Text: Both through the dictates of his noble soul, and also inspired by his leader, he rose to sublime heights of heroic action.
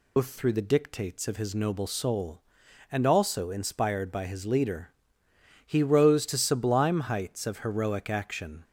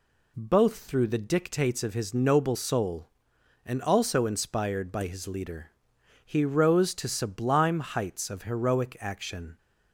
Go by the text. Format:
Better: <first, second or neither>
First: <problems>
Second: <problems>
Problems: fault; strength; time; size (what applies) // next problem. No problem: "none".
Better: second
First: loses the start of "Both"; at 0.1 s; 150 ms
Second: none